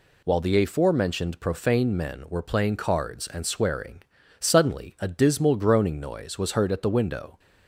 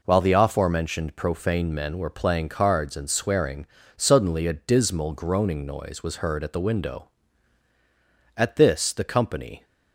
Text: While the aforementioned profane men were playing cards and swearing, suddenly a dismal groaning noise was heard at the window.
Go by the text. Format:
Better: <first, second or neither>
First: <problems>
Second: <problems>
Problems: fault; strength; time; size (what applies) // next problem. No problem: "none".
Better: first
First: none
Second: goes on to say "At this the company"; noticeable; from 8.3 s on; 1.2 s long